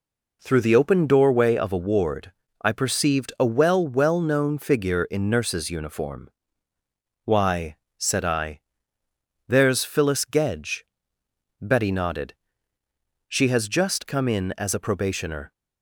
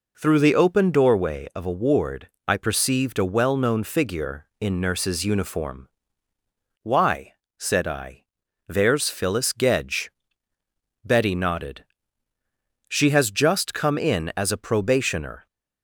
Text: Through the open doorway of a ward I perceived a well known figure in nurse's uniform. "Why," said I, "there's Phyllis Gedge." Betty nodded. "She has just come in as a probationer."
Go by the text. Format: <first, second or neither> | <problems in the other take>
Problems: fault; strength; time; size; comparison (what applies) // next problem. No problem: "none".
second | pauses between "ward" and "I"; slight; at 2.3 s; 0.30 s long; slight in the second // says "well" twice; at 3.8 s